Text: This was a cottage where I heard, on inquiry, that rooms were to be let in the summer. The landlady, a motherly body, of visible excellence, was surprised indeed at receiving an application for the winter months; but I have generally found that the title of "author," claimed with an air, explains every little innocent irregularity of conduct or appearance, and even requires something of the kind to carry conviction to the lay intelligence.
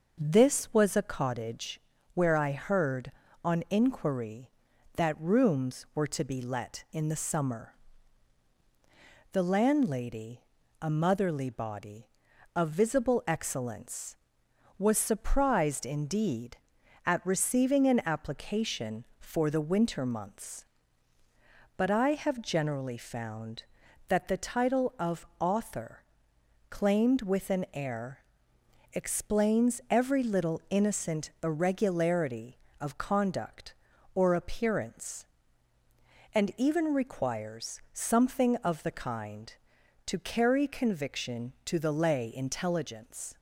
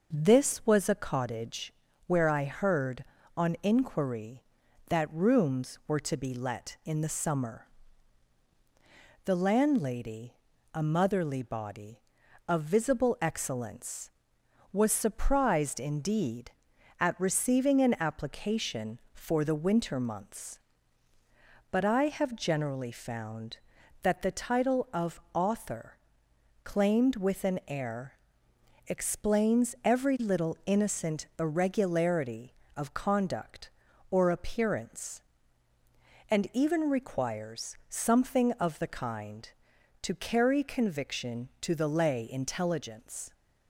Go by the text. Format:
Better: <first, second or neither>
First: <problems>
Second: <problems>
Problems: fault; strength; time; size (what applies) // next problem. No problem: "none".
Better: neither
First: pauses between "cottage" and "where"; slight; at 1.7 s; 0.34 s long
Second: pauses between "cottage" and "where"; slight; at 1.7 s; 0.34 s long